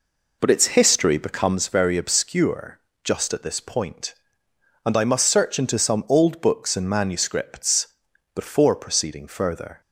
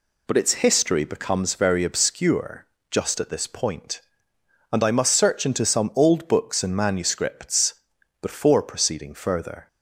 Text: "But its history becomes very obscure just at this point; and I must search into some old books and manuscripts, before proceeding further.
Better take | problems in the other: second | starts louder than the rest; until 1.6 s; 4 dB // pauses between "obscure" and "just"; slight; at 2.7 s; 0.24 s long; slight in the second

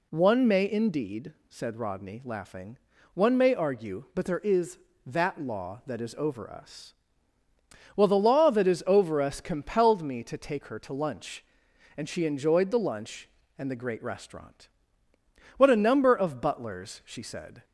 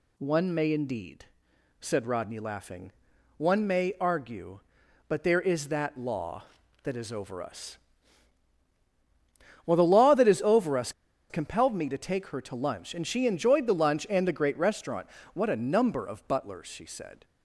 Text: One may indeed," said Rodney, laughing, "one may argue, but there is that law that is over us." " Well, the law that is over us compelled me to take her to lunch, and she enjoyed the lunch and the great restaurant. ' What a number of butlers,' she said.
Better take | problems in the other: first | pauses between "us" and "compelled"; at 10.9 s; 0.38 s long

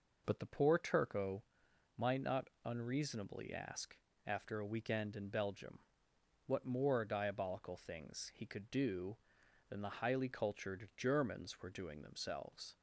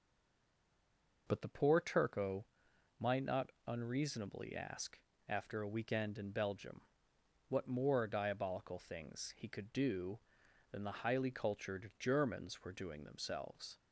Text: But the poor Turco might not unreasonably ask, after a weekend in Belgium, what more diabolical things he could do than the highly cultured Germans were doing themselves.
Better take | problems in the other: first | stays silent before the first word; noticeable; until 1.2 s; 1.2 s long // pauses between "Turco" and "might"; noticeable; at 2.4 s; 0.54 s long; noticeable in the first

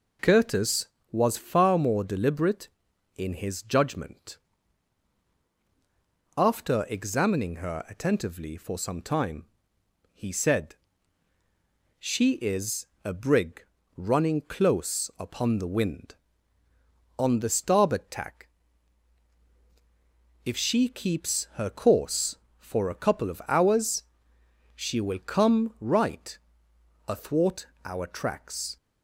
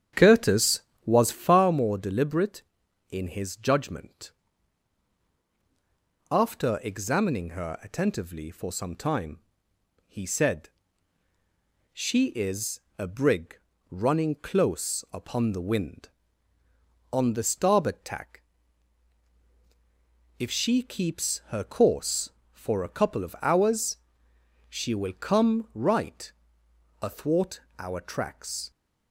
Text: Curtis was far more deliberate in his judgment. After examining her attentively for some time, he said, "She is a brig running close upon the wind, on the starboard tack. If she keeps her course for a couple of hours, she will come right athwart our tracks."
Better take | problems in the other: first | starts louder than the rest; strong; until 1.8 s; 9 dB // pauses between "is" and "a"; slight; at 12.8 s; 0.16 s long; slight in the first // pauses between "brig" and "running"; slight; at 13.5 s; 0.32 s long; slight in the first // pauses between "right" and "athwart"; noticeable; at 26.3 s; 0.72 s long; noticeable in the first // pauses between "athwart" and "our"; slight; at 27.6 s; 0.20 s long; slight in the first

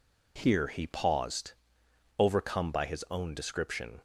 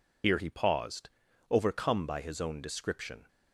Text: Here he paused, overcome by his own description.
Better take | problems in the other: first | loses the start of "Here"; at 0.2 s; 80 ms

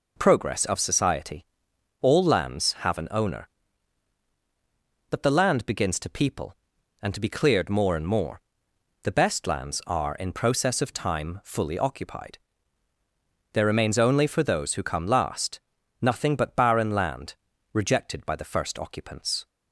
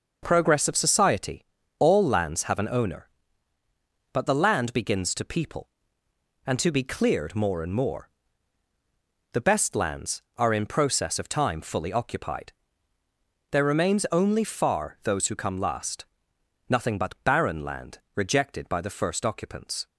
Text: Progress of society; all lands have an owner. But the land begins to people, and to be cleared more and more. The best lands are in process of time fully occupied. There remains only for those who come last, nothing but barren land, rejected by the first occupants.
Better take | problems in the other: first | says "far" for "for"; at 14.4 s

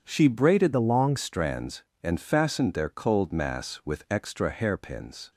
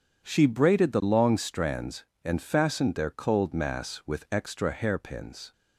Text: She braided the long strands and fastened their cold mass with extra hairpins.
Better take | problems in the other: second | changes voice from "the" to "long"; from 0.7 to 1.1 s; 0.4 s long

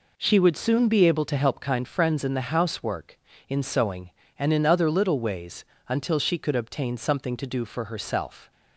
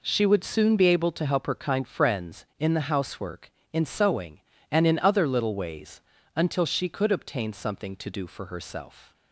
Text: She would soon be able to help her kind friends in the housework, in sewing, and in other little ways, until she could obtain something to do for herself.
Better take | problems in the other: second | skips "her"; at 1.5 s

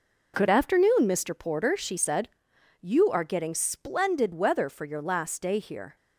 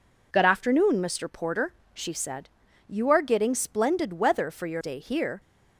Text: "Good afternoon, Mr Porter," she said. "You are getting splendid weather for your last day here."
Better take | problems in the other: first | skips "last"; at 4.8 s

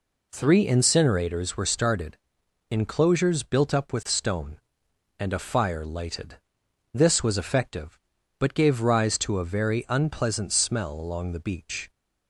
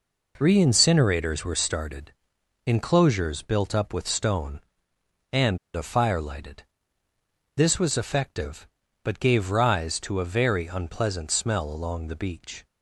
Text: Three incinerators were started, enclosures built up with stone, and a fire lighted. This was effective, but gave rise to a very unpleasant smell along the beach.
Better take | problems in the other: first | pauses between "and" and "a"; slight; at 5.5 s; 0.19 s long

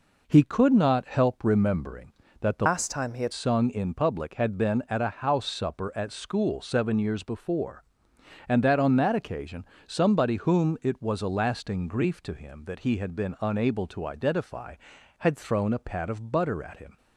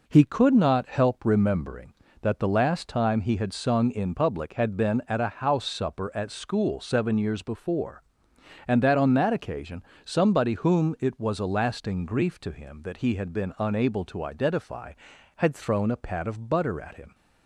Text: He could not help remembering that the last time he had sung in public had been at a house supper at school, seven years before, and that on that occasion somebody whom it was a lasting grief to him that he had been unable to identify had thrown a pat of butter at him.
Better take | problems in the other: second | changes voice from "last" to "had"; from 2.6 to 3.3 s; 0.7 s long // pauses between "occasion" and "somebody"; slight; at 9.6 s; 0.22 s long; slight in the second

